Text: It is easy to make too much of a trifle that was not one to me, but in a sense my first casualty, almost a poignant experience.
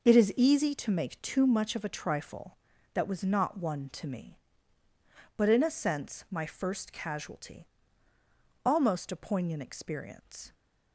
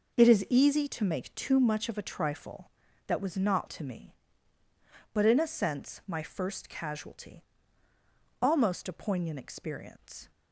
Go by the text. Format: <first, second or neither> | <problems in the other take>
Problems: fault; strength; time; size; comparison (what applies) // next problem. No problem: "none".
first | skips "one"; at 3.6 s